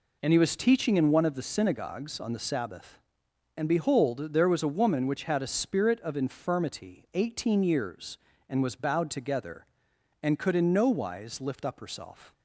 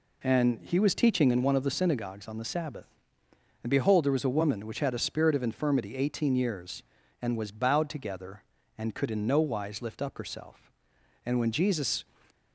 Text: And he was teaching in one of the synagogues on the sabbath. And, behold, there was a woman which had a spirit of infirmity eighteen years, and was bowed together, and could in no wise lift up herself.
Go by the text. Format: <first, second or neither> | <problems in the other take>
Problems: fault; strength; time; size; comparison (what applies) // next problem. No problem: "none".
first | goes on to say "And when Jesus"; noticeable; from 11.2 s on; 0.80 s long